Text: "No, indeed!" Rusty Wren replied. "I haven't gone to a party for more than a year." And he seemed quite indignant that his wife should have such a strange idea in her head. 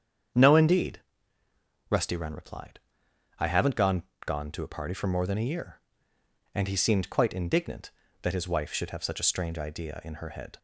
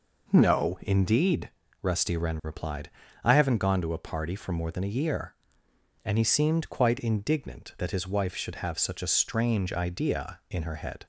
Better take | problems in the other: second | starts louder than the rest; strong; until 2.2 s; 8 dB // says "gone" twice; at 4.2 s

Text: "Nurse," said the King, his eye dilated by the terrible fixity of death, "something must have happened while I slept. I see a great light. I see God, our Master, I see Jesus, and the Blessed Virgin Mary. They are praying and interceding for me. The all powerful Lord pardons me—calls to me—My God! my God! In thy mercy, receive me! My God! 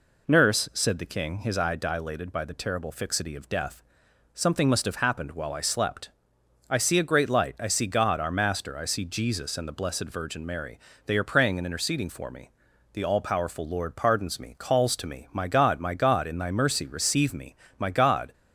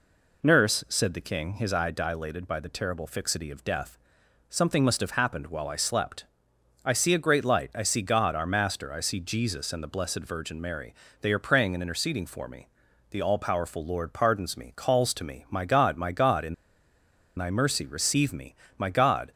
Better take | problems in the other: first | pauses between "In" and "thy"; noticeable; at 16.5 s; 0.83 s long

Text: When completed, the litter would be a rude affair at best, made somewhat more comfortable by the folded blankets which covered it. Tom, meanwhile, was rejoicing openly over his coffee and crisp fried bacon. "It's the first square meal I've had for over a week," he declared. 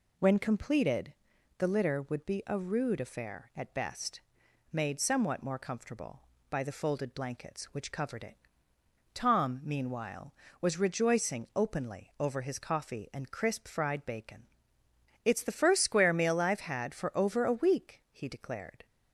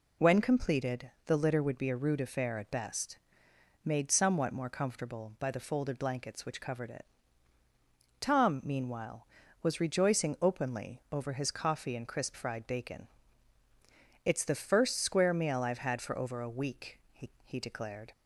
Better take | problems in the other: first | says "he" twice; at 17.4 s

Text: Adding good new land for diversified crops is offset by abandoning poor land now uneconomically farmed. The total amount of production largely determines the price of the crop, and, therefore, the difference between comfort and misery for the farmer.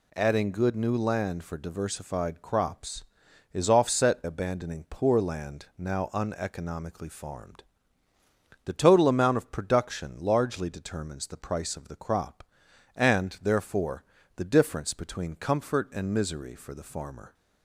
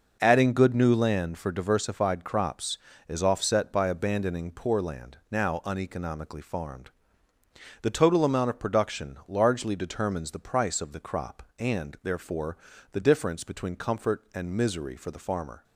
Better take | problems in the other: second | skips "by"; at 4.2 s

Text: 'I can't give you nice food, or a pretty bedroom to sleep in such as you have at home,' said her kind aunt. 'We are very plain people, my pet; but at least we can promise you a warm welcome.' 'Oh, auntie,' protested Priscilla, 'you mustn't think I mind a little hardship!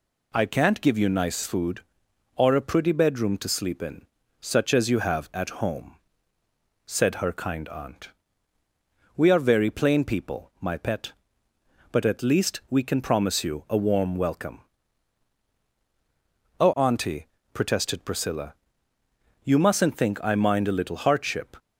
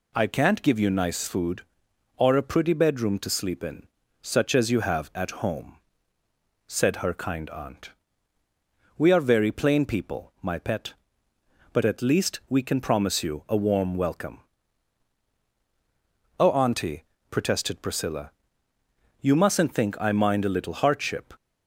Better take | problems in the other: neither | pauses between "in" and "such"; slight; the same in both

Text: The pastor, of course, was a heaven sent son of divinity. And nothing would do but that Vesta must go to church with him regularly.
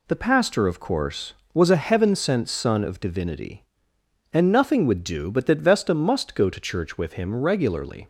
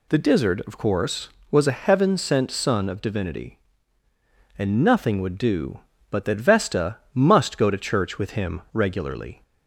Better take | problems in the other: first | says "dizzard" for "pastor"; at 0.1 s // pauses between "Vesta" and "must"; slight; at 6.9 s; 0.16 s long

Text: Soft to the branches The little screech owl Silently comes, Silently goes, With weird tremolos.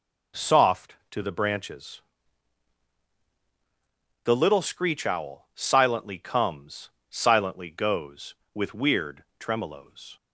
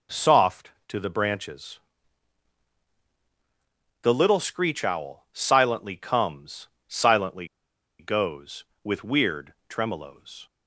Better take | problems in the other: first | pauses between "branches" and "The"; strong; at 1.7 s; 2.2 s long; strong in the first // pauses between "Silently" and "goes"; noticeable; at 7.4 s; 0.53 s long

